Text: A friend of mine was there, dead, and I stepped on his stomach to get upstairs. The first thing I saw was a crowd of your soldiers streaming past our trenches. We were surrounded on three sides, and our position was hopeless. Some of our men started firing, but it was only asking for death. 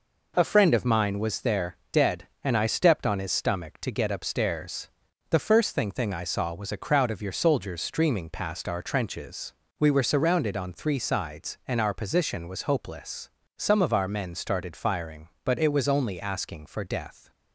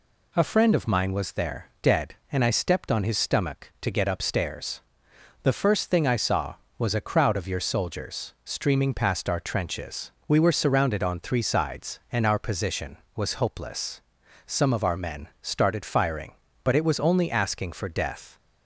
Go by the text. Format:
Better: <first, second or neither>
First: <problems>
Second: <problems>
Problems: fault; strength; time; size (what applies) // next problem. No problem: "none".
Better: second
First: says "thing" twice; at 5.9 s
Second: none